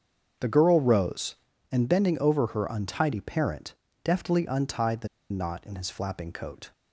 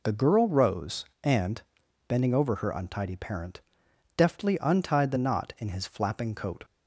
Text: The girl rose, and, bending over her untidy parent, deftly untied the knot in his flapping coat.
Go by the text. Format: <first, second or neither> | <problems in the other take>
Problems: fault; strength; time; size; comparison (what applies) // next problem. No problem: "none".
second | starts louder than the rest; until 1.7 s; 7 dB // pauses between "the" and "knot"; slight; at 5.0 s; 0.22 s long